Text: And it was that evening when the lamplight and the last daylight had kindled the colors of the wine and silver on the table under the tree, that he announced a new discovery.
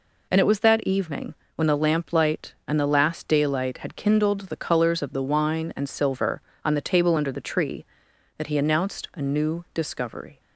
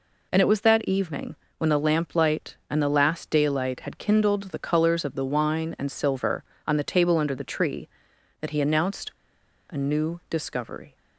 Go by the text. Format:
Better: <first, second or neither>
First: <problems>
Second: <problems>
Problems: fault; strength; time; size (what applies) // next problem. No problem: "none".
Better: first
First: pauses between "evening" and "when"; slight; at 1.3 s; 0.20 s long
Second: pauses between "evening" and "when"; slight; at 1.3 s; 0.22 s long // pauses between "announced" and "a"; noticeable; at 9.1 s; 0.58 s long